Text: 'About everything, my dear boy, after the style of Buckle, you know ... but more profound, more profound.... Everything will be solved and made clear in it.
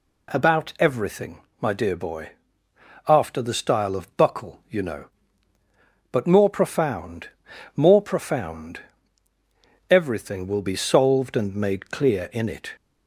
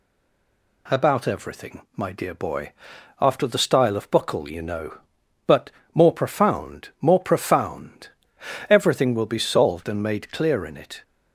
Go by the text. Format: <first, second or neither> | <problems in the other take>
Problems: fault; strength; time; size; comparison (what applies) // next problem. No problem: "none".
first | stays silent before the first word; slight; until 0.8 s; 0.8 s long // pauses between "but" and "more"; slight; at 5.6 s; 0.26 s long